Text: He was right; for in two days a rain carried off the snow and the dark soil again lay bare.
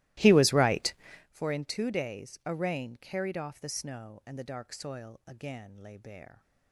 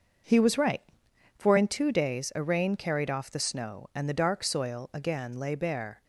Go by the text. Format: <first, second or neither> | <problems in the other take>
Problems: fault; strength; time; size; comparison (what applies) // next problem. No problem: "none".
second | starts louder than the rest; strong; until 1.3 s; 17.5 dB